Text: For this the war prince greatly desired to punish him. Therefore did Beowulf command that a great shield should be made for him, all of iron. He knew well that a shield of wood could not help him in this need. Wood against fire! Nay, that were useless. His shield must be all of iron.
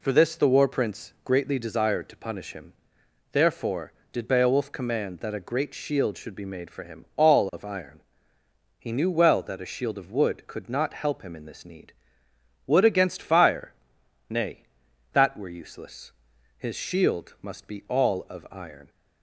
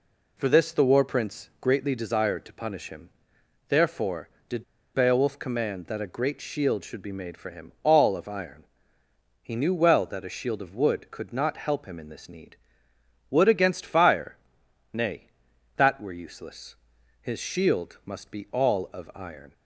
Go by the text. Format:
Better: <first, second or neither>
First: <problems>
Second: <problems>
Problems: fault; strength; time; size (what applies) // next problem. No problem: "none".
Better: first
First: none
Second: pauses between "did" and "Beowulf"; slight; at 4.6 s; 0.32 s long